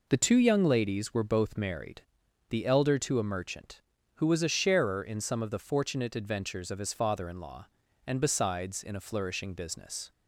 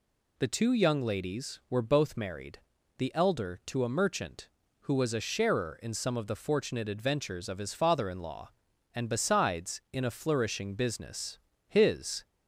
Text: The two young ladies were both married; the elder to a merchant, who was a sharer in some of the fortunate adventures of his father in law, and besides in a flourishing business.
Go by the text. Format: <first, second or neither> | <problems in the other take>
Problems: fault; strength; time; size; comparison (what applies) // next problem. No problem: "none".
first | goes on to say "His"; from 11.6 s on; 0.58 s long